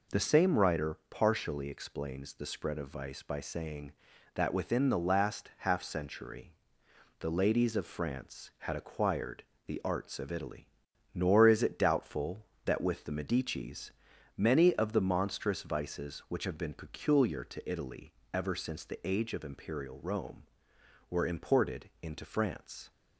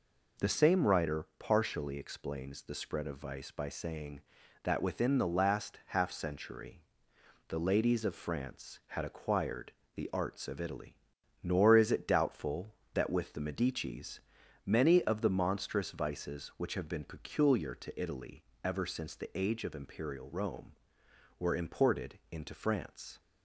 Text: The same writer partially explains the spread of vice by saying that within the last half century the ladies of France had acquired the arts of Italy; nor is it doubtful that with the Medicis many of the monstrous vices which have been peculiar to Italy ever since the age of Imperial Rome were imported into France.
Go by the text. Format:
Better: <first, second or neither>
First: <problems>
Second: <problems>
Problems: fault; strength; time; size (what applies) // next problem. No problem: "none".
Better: neither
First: pauses between "century" and "the"; noticeable; at 6.5 s; 0.64 s long // pauses between "acquired" and "the"; slight; at 9.4 s; 0.24 s long // pauses between "Medicis" and "many"; at 13.9 s; 0.44 s long // pauses between "Italy" and "ever"; slight; at 18.1 s; 0.20 s long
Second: pauses between "century" and "the"; noticeable; at 6.8 s; 0.64 s long // pauses between "acquired" and "the"; slight; at 9.7 s; 0.24 s long // pauses between "Medicis" and "many"; at 14.1 s; 0.44 s long // pauses between "Italy" and "ever"; slight; at 18.4 s; 0.20 s long